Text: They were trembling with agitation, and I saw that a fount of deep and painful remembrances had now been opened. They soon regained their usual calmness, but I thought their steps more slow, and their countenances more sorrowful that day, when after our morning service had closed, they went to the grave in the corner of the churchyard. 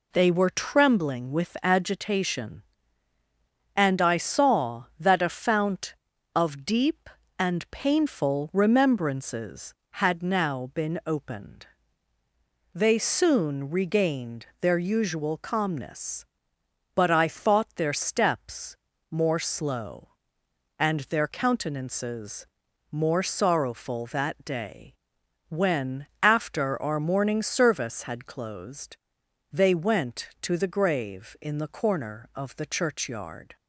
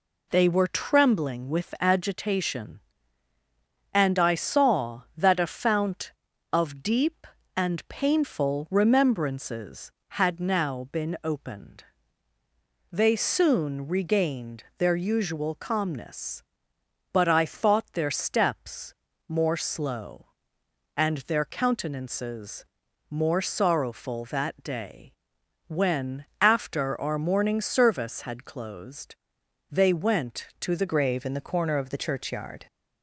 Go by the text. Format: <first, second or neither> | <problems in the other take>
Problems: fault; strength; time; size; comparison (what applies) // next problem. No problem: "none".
first | pauses between "steps" and "more"; at 18.9 s; 0.38 s long; also in the first // pauses between "countenances" and "more"; at 22.6 s; 0.44 s long; also in the first // pauses between "when" and "after"; slight; at 26.2 s; 0.16 s long; slight in the first // changes voice at "grave"; from 30.8 s on; 1.8 s long